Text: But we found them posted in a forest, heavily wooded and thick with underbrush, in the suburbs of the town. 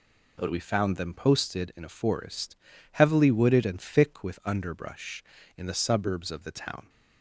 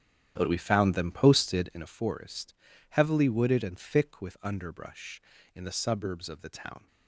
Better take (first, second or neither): first